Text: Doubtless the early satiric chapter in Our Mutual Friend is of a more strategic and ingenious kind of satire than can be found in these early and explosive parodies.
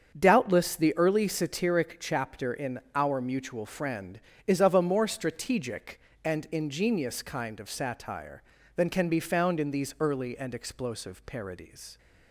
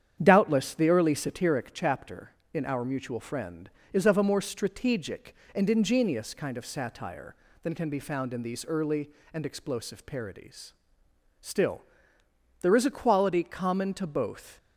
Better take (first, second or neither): first